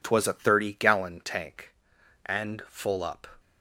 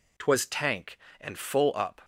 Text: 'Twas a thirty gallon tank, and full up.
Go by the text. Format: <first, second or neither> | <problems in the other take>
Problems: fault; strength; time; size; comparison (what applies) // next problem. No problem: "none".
first | skips "a thirty gallon"; at 0.4 s